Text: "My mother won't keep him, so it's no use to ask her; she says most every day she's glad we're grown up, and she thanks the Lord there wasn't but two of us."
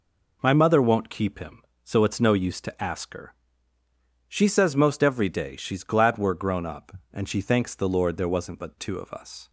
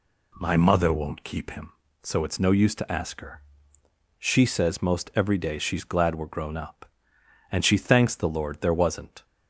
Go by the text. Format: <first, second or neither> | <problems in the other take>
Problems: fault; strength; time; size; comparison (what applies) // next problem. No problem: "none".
first | stops before "but two of us"; at 9.2 s